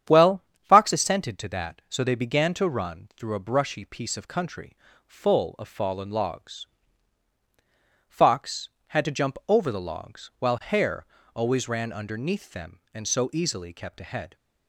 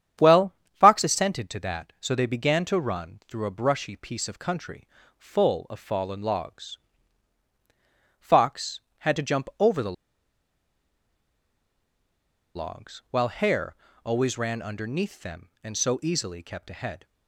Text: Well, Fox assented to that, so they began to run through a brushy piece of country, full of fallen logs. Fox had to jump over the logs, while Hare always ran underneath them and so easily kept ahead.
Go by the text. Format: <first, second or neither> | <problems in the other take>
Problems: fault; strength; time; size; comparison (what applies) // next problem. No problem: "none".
first | starts louder than the rest; strong; until 1.4 s; 9 dB; strong in the first // pauses between "the" and "logs"; strong; at 9.9 s; 2.6 s long // pauses between "Hare" and "always"; slight; at 13.7 s; 0.30 s long; slight in the first